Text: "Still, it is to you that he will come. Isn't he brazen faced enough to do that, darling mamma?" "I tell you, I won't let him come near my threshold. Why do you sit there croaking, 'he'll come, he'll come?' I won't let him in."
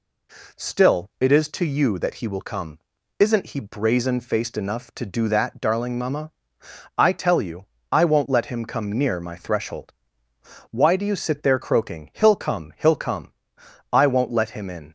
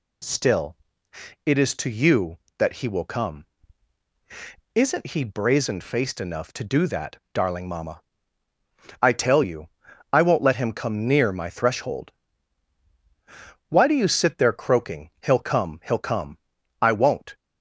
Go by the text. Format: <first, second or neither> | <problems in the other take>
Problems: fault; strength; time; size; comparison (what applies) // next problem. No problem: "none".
first | stops before "let him in"; at 17.3 s